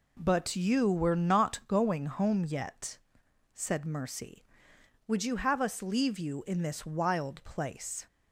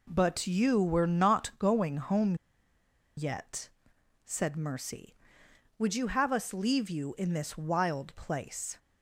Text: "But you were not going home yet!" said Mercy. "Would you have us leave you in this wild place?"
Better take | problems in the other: first | pauses between "home" and "yet"; noticeable; at 2.3 s; 0.82 s long

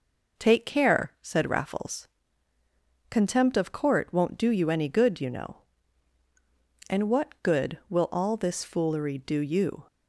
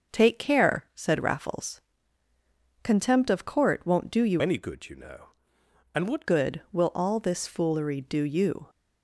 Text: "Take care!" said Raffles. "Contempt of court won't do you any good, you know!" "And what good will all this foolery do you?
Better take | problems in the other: first | starts louder than the rest; until 1.2 s; 6.5 dB // changes voice from "any" to "what"; from 4.3 to 6.2 s; 1.9 s long

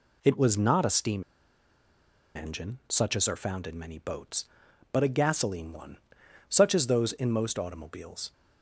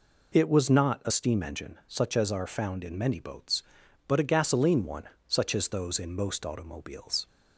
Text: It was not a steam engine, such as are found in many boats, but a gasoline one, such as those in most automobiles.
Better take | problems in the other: second | pauses between "steam" and "engine"; at 1.2 s; 1.1 s long

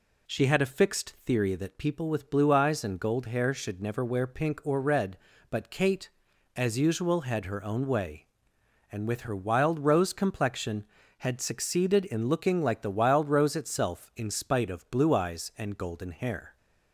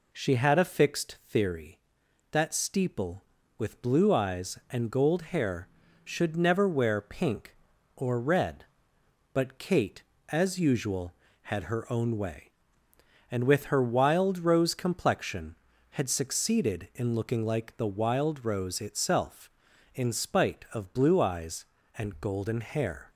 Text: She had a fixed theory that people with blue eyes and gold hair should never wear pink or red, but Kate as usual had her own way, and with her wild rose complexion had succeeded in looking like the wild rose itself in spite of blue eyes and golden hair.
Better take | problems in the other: first | says "steeple" for "people"; at 2.5 s

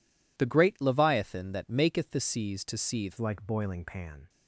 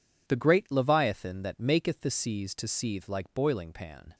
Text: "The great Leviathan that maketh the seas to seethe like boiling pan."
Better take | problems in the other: second | changes voice at "like"; from 3.1 s on; 1.1 s long

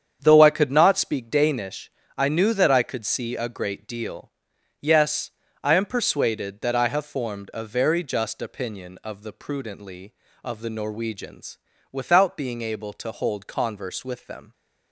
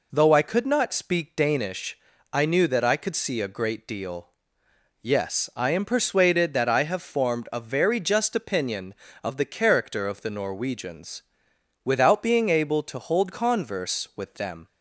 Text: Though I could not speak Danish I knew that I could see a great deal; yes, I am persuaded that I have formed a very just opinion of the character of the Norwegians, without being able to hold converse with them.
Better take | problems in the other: second | starts louder than the rest; strong; until 1.2 s; 8 dB // pauses between "Danish" and "I"; slight; at 1.8 s; 0.28 s long; slight in the second // says "prudently" for "character"; at 9.3 s

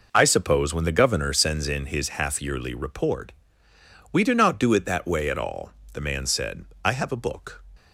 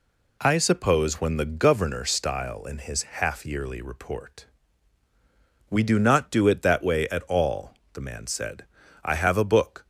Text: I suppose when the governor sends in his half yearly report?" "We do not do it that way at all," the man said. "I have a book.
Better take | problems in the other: first | says "style" for "sends"; at 2.0 s

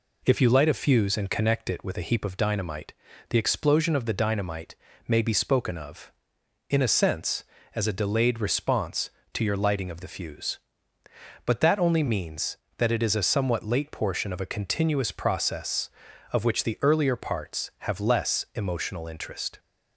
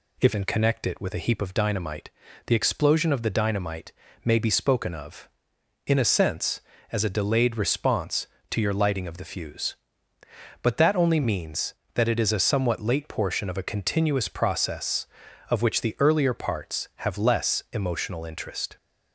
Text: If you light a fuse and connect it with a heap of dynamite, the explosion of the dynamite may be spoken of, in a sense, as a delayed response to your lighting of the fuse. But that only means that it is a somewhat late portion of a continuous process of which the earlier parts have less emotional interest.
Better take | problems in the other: first | skips "you light a fuse"; at 0.3 s // pauses between "dynamite" and "may"; slight; at 3.9 s; 0.32 s long; slight in the first

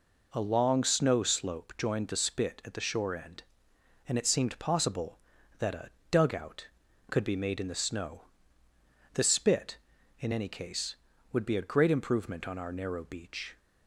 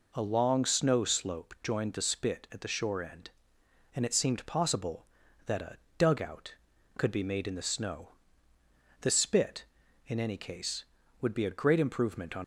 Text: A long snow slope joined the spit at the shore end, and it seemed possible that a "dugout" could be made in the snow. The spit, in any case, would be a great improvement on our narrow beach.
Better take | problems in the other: first | pauses between "a" and "dugout"; slight; at 5.7 s; 0.20 s long; slight in the first // stops before "our narrow beach"; at 12.4 s

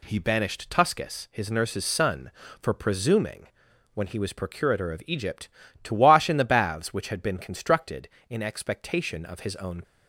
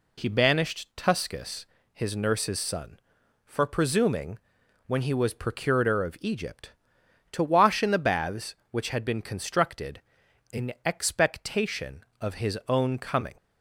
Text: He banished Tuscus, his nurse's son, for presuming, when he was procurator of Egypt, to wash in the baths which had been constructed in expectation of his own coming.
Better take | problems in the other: second | stops before "coming"; at 9.8 s

